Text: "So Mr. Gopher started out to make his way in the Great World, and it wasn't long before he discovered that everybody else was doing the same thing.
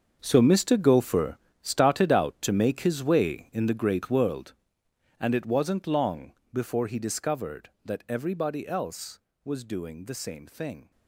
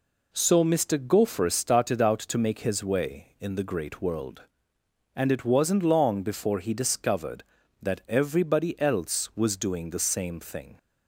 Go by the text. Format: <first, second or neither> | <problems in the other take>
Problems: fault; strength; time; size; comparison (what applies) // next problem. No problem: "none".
second | gets quieter; strong; throughout; 13.5 dB // pauses between "Gopher" and "started"; slight; at 1.3 s; 0.24 s long // pauses between "long" and "before"; slight; at 6.3 s; 0.20 s long